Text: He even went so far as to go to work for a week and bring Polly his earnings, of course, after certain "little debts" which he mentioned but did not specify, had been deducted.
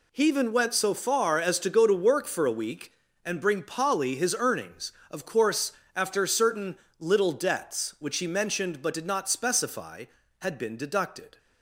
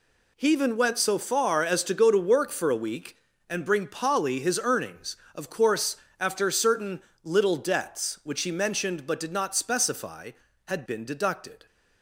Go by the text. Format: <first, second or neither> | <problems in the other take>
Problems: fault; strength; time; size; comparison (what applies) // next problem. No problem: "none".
neither | pauses between "certain" and "little"; slight; the same in both